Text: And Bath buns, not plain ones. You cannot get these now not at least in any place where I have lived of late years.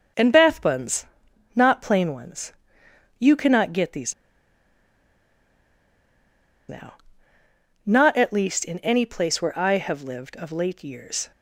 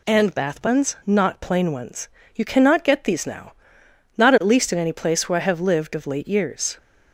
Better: second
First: pauses between "these" and "now"; strong; at 4.1 s; 2.5 s long // pauses between "now" and "not"; noticeable; at 6.9 s; 0.92 s long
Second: pauses between "now" and "not"; noticeable; at 3.5 s; 0.62 s long

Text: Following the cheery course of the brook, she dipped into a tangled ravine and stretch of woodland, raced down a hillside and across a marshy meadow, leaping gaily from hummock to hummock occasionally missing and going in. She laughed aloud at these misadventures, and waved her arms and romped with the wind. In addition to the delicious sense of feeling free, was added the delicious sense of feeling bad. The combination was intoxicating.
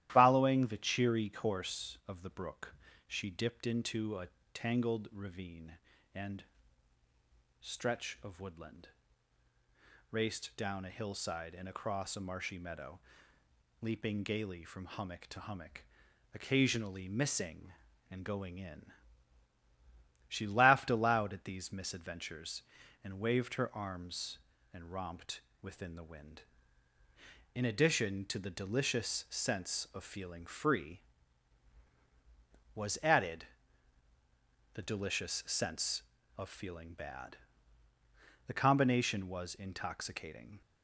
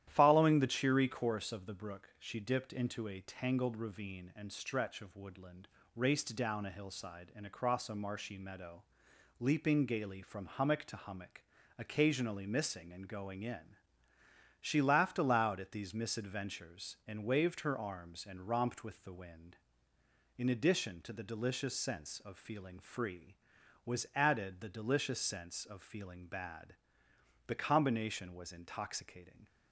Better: second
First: starts louder than the rest; strong; until 1.1 s; 13.5 dB // pauses between "a" and "tangled"; slight; at 4.2 s; 0.26 s long // pauses between "and" and "stretch"; at 6.4 s; 1.1 s long // pauses between "hummock" and "occasionally"; noticeable; at 15.8 s; 0.50 s long // says "within" for "with"; at 25.6 s // pauses between "added" and "the"; strong; at 33.4 s; 1.3 s long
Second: starts louder than the rest; strong; until 1.0 s; 11.5 dB // pauses between "hummock" and "occasionally"; at 11.4 s; 0.38 s long

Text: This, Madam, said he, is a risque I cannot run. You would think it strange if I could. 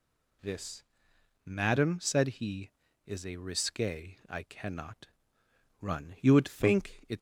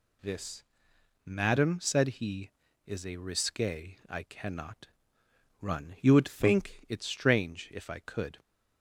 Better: second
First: pauses between "cannot" and "run"; noticeable; at 5.0 s; 0.74 s long // stops before "strange if I could"; at 7.1 s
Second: pauses between "cannot" and "run"; noticeable; at 4.8 s; 0.74 s long

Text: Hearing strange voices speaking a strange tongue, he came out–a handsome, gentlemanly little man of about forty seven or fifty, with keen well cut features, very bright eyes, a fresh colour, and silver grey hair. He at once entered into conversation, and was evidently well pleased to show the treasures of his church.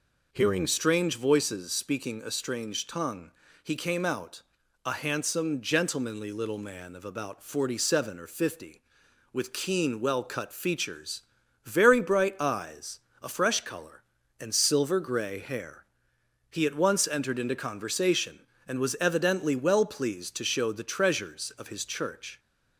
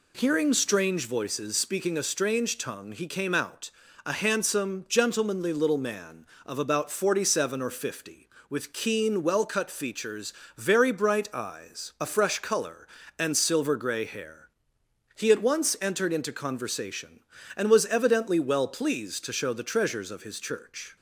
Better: neither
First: none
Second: none

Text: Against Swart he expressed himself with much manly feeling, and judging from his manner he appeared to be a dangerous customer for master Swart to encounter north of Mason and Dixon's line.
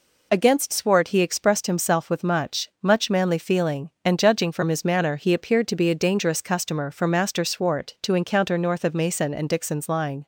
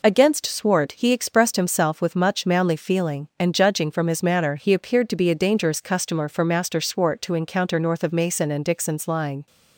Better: second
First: says "much" twice; at 2.8 s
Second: none

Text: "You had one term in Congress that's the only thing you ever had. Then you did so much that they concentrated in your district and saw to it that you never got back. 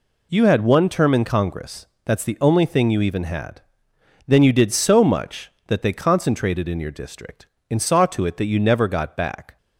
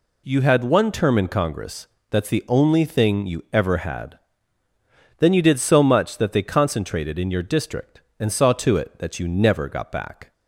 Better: second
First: pauses between "Congress" and "that's"; slight; at 1.8 s; 0.18 s long // says "even" for "ever"; at 3.0 s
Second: pauses between "Congress" and "that's"; slight; at 1.8 s; 0.22 s long

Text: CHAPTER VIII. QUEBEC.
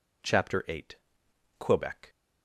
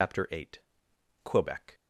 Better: first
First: none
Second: loses the start of "CHAPTER"; at 0.0 s; 145 ms

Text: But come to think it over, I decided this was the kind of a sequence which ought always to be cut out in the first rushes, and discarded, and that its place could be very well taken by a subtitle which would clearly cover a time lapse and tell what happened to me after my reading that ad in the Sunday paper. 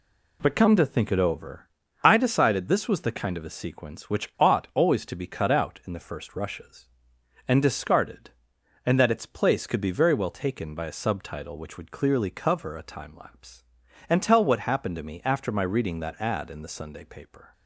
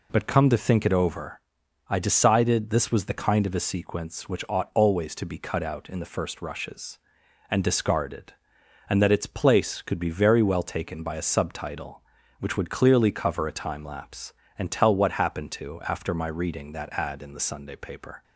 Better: first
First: none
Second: skips "me"; at 15.8 s

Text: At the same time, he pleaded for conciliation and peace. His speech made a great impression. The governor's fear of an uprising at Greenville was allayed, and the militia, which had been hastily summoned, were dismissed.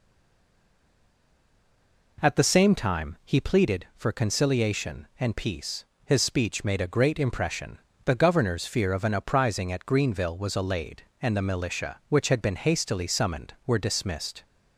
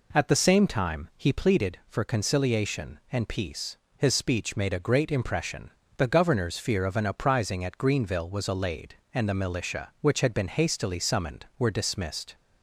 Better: second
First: stays silent before the first word; until 2.1 s; 2.1 s long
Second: none

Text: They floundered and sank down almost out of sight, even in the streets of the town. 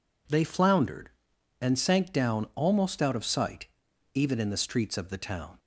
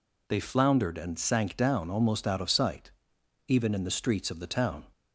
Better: neither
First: none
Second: none

